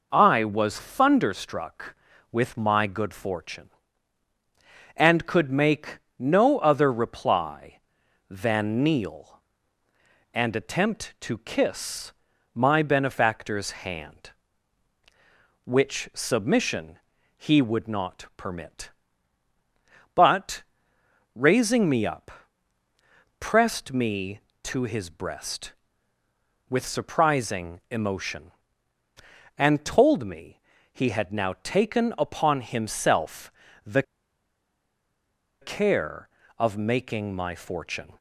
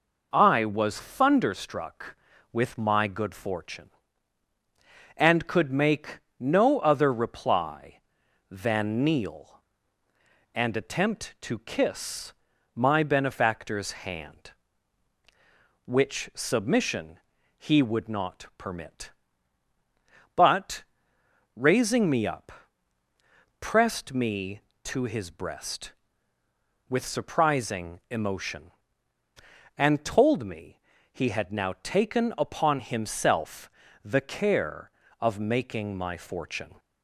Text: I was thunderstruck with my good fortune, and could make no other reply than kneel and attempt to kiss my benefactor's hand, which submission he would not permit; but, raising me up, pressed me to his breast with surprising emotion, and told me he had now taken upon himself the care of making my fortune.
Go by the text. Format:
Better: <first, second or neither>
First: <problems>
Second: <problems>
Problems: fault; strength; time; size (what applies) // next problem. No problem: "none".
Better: second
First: pauses between "make" and "no"; slight; at 5.9 s; 0.20 s long // pauses between "kiss" and "my"; at 12.1 s; 0.44 s long // pauses between "submission" and "he"; at 16.9 s; 0.38 s long // pauses between "me" and "he"; slight; at 30.6 s; 0.32 s long // pauses between "himself" and "the"; slight; at 33.5 s; 0.34 s long // pauses between "the" and "care"; strong; at 34.0 s; 1.5 s long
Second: pauses between "make" and "no"; slight; at 6.1 s; 0.20 s long // pauses between "kiss" and "my"; at 12.3 s; 0.44 s long // pauses between "submission" and "he"; at 17.1 s; 0.38 s long // pauses between "me" and "he"; slight; at 30.8 s; 0.32 s long // pauses between "himself" and "the"; slight; at 33.6 s; 0.34 s long